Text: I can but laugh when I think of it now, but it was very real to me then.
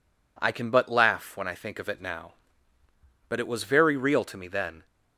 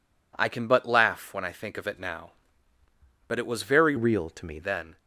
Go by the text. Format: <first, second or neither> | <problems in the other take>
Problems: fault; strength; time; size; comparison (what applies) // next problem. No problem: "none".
first | changes voice from "real" to "me"; from 3.9 to 4.5 s; 0.6 s long